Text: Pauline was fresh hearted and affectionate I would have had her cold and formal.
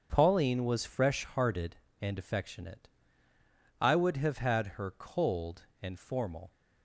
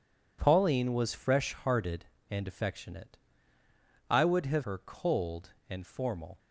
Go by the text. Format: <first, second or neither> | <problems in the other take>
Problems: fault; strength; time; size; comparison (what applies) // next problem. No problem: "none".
first | pauses between "affectionate" and "I"; noticeable; at 3.1 s; 0.92 s long; noticeable in the first // skips "had"; at 4.6 s